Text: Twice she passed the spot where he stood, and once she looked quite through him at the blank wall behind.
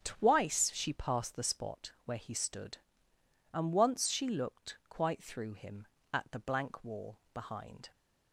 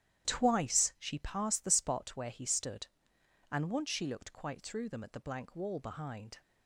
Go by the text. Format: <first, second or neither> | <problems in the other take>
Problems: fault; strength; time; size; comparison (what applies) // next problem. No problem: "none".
first | starts louder than the rest; strong; until 1.3 s; 11.5 dB; strong in the first // says "them" for "him"; at 4.8 s